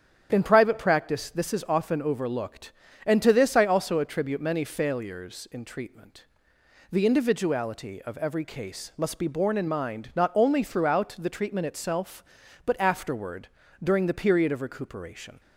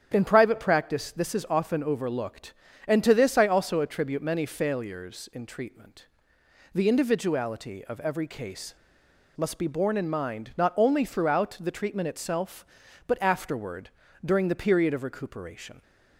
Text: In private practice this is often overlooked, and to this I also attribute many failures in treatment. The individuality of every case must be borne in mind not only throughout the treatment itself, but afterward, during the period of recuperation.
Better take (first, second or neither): first